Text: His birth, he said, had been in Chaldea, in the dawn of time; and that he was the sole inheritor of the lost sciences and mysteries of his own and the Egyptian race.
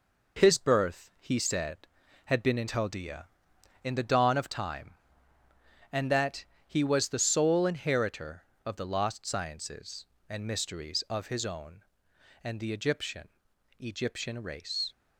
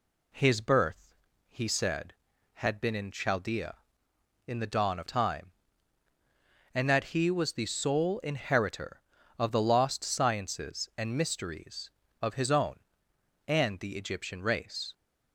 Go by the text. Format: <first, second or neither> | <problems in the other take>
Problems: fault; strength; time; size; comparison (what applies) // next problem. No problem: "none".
second | pauses between "that" and "he"; slight; at 6.4 s; 0.24 s long // says "Egyptian" twice; at 13.7 s